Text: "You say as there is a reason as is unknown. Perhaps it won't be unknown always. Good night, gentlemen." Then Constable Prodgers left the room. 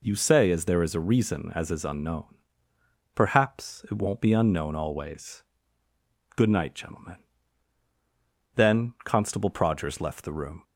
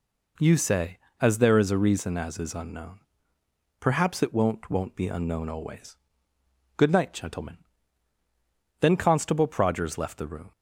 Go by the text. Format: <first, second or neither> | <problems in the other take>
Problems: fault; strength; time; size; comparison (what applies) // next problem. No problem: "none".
first | says "won't" twice; at 4.6 s